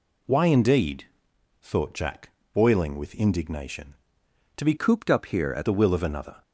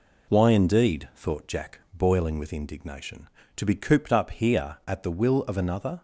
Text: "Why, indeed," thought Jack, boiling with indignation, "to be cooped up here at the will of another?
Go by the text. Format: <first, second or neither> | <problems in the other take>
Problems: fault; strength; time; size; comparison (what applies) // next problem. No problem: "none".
second | changes voice from "cooped" to "at"; from 4.7 to 5.6 s; 0.9 s long